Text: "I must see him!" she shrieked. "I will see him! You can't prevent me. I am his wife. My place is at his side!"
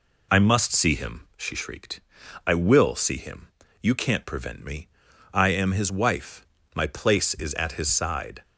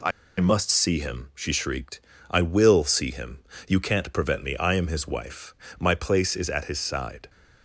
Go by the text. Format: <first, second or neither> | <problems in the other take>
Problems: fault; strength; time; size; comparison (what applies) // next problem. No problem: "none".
first | pauses between "I" and "must"; slight; at 0.1 s; 0.30 s long